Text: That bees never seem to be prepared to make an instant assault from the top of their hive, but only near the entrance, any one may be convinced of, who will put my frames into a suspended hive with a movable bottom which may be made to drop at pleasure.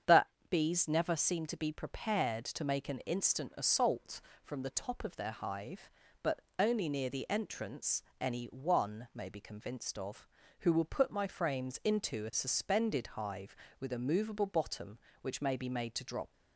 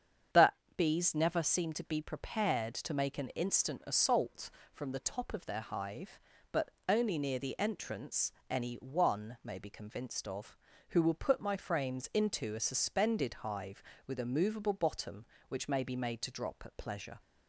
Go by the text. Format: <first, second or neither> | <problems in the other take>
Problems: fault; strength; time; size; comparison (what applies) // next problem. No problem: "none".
second | starts louder than the rest; strong; until 1.3 s; 7.5 dB; strong in the second // pauses between "That" and "bees"; slight; at 0.2 s; 0.24 s long; slight in the second // pauses between "but" and "only"; slight; at 6.4 s; 0.18 s long; slight in the second // stops before "at pleasure"; at 16.3 s